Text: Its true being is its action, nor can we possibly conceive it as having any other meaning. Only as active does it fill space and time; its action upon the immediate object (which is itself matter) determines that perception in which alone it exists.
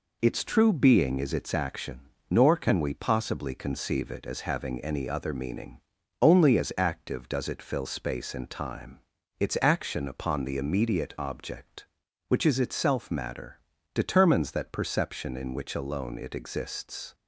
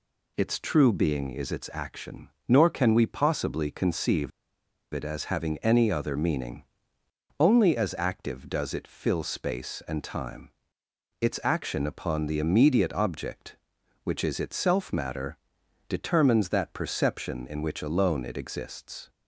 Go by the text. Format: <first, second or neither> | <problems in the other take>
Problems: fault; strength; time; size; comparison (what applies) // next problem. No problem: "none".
first | pauses between "conceive" and "it"; noticeable; at 4.3 s; 0.63 s long